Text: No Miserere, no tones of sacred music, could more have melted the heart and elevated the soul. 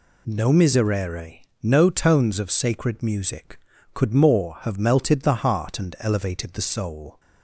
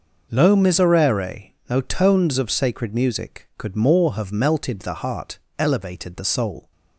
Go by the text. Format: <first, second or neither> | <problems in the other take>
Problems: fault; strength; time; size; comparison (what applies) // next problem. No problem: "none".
first | skips "and"; at 5.4 s